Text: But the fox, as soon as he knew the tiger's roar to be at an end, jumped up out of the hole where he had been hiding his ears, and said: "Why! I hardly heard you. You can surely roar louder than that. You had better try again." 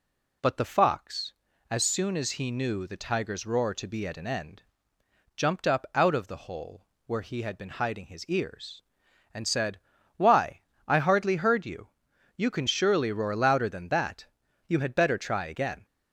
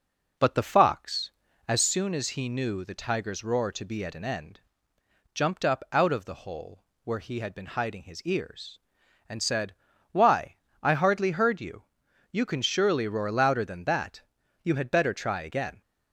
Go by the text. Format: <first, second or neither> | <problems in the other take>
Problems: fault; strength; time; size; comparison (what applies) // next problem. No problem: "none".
first | starts louder than the rest; noticeable; until 2.0 s; 5 dB // pauses between "hole" and "where"; slight; at 6.8 s; 0.20 s long; slight in the first